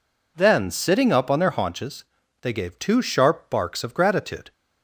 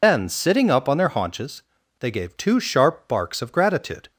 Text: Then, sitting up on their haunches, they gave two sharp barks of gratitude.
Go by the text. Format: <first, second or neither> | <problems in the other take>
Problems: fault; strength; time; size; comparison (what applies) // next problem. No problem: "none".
first | loses the start of "Then"; at 0.0 s; 85 ms